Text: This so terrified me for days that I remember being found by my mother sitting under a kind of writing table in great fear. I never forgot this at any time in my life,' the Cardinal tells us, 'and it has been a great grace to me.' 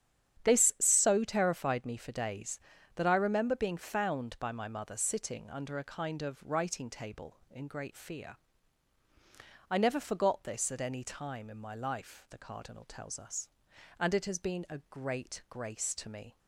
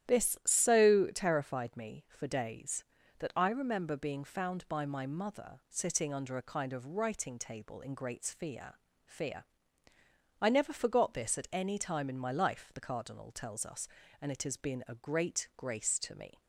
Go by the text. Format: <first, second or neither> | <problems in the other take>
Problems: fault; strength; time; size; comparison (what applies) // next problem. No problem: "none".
first | starts louder than the rest; strong; until 1.2 s; 11.5 dB; strong in the first // says "fear" twice; at 9.0 s